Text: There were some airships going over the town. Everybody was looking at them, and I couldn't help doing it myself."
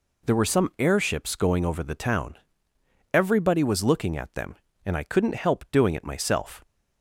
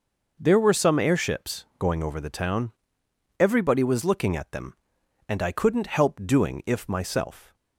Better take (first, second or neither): first